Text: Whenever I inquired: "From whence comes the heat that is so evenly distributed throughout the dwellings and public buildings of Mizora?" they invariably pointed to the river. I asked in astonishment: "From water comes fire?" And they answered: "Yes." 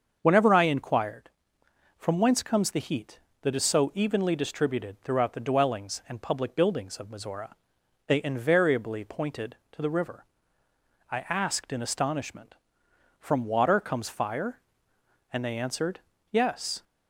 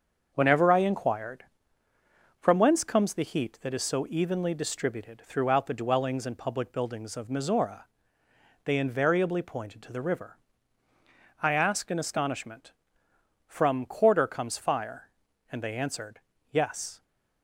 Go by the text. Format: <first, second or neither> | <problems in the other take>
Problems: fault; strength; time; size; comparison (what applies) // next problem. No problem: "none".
first | starts louder than the rest; until 1.3 s; 6.5 dB; also in the first // says "quarter" for "water"; at 13.8 s